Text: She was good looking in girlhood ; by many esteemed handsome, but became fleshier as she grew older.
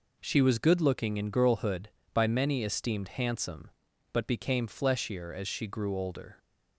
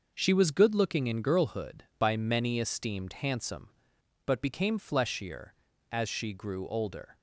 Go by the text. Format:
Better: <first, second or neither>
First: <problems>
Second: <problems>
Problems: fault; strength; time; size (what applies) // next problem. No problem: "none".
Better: neither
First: none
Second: none